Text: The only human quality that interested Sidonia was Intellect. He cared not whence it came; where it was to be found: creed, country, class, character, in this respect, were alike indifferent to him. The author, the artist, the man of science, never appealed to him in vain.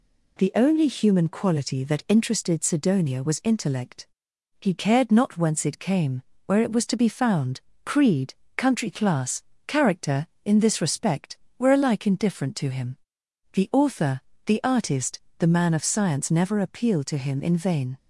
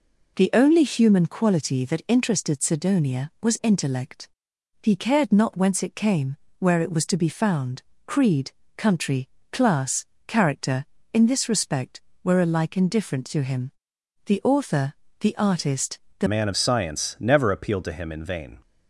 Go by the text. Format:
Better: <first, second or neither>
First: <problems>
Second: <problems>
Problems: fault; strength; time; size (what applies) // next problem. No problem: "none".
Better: first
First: none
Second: changes voice at "man"; from 16.2 s on; 2.3 s long